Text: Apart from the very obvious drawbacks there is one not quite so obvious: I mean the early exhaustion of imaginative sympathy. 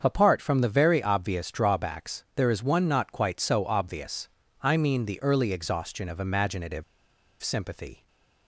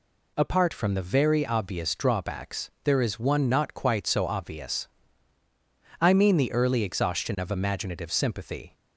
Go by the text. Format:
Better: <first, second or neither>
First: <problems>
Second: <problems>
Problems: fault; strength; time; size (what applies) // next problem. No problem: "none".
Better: second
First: starts louder than the rest; until 1.0 s; 7 dB // pauses between "imaginative" and "sympathy"; noticeable; at 6.8 s; 0.58 s long // stays silent after the last word; slight; from 7.9 s on; 0.5 s long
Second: none